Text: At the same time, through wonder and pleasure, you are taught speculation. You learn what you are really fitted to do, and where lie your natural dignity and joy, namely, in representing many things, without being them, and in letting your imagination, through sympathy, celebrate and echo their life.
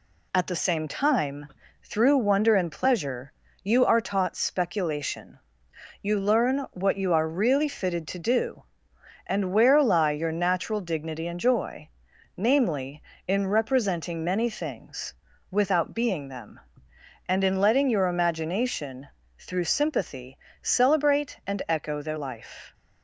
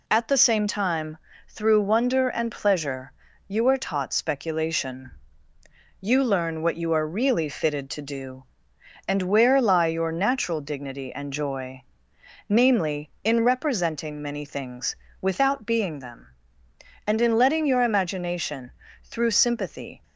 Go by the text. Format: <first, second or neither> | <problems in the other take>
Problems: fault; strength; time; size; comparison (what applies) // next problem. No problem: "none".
first | stops before "celebrate and echo their life"; at 20.0 s